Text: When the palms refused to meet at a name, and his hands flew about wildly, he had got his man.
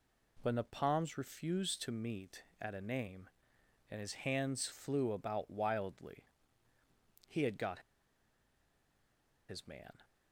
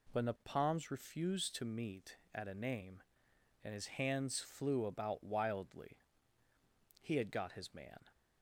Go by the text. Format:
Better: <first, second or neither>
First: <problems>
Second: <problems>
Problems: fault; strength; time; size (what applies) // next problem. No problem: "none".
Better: second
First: pauses between "got" and "his"; strong; at 7.7 s; 1.6 s long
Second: none